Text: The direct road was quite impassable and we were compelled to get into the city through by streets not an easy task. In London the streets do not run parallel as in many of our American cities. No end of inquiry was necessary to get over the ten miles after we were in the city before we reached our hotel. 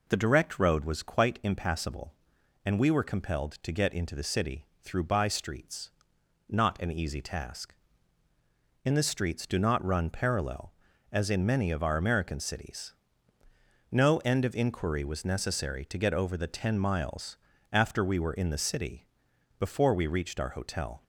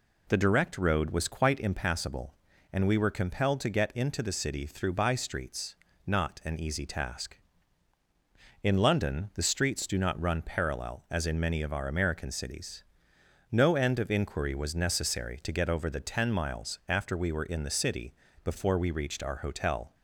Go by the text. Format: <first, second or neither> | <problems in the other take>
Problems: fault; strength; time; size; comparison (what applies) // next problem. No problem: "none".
second | pauses between "city" and "through"; slight; at 4.6 s; 0.16 s long // pauses between "streets" and "not"; noticeable; at 5.9 s; 0.58 s long; slight in the second // skips "London"; at 8.9 s // pauses between "miles" and "after"; slight; at 17.3 s; 0.36 s long // pauses between "city" and "before"; noticeable; at 19.0 s; 0.52 s long; slight in the second